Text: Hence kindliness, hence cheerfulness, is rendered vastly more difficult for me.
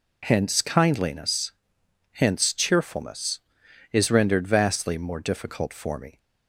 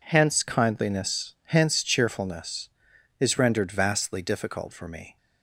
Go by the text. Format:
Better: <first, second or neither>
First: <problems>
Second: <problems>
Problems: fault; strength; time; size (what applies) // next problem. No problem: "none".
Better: first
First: none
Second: skips "more"; at 4.2 s